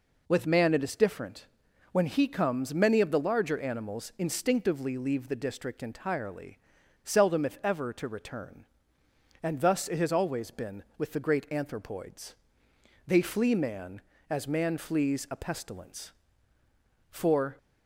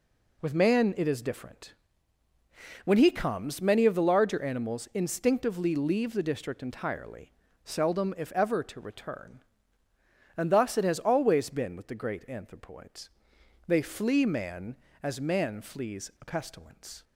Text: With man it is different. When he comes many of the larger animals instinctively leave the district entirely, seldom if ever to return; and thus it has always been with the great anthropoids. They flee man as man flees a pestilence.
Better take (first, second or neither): second